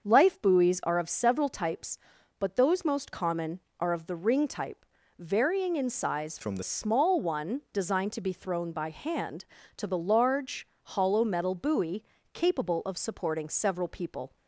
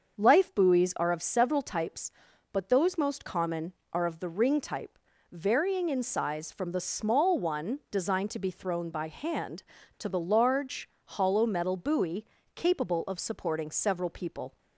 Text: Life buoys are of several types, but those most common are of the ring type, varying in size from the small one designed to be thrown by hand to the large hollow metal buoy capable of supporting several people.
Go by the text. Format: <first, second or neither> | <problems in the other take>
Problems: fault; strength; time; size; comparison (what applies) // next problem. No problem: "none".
second | starts louder than the rest; until 1.0 s; 6.5 dB; also in the second // changes voice from "from" to "the"; from 6.4 to 6.6 s; 0.2 s long // pauses between "large" and "hollow"; slight; at 10.6 s; 0.16 s long; slight in the second // pauses between "buoy" and "capable"; slight; at 12.0 s; 0.30 s long; slight in the second